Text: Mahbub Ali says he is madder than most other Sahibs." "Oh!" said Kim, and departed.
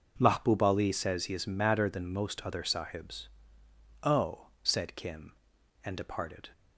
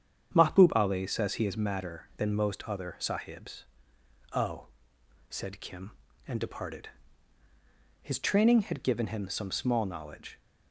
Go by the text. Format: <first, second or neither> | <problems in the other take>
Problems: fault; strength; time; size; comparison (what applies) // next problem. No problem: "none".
first | starts louder than the rest; strong; until 1.3 s; 8.5 dB // goes on to say "His training had given him some small knowledge"; strong; from 8.0 s on; 2.3 s long